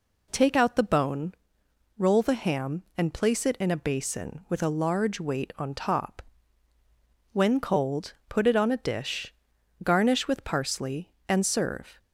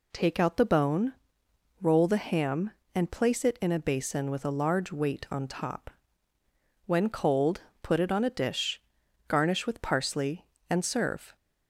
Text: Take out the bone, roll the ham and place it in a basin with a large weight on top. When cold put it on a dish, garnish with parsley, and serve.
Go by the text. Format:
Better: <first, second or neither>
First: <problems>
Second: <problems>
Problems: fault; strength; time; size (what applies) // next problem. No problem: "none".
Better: neither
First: pauses between "cold" and "put"; slight; at 8.1 s; 0.16 s long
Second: pauses between "cold" and "put"; slight; at 7.6 s; 0.22 s long